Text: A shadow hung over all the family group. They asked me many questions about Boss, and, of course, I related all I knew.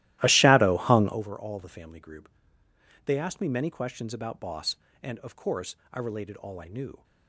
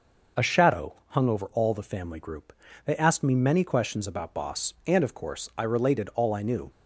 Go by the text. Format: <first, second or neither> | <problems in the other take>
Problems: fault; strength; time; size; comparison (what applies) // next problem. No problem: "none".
second | starts louder than the rest; strong; until 1.2 s; 15.5 dB